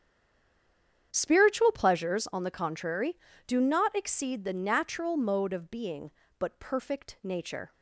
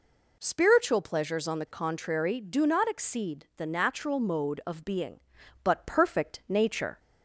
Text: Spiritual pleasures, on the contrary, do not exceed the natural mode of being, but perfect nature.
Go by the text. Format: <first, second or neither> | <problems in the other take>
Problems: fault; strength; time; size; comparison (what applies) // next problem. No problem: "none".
second | stays silent before the first word; until 1.1 s; 1.1 s long // starts louder than the rest; strong; until 2.1 s; 8.5 dB